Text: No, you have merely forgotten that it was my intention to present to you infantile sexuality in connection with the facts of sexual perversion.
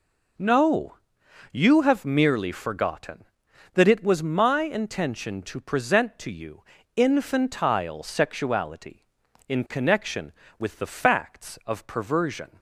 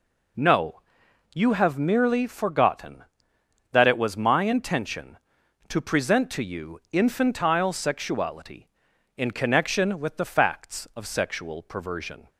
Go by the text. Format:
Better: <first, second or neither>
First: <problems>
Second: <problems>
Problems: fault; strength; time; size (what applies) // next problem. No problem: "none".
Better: second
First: pauses between "you" and "infantile"; slight; at 6.6 s; 0.34 s long // skips "sexual"; at 11.8 s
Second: none